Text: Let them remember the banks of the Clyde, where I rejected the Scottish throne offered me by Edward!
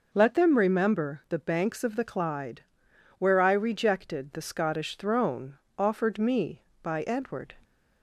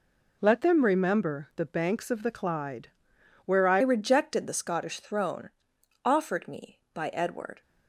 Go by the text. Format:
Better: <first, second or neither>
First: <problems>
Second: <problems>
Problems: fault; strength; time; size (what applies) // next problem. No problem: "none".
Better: first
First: pauses between "throne" and "offered"; slight; at 5.5 s; 0.22 s long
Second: changes voice at "rejected"; from 3.8 s on; 3.8 s long // pauses between "throne" and "offered"; noticeable; at 5.5 s; 0.52 s long